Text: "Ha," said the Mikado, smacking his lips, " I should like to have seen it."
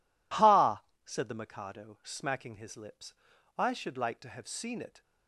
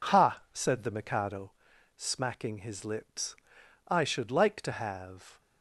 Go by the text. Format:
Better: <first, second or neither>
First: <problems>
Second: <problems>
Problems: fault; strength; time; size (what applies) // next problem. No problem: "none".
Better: first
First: none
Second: stops before "seen it"; at 5.3 s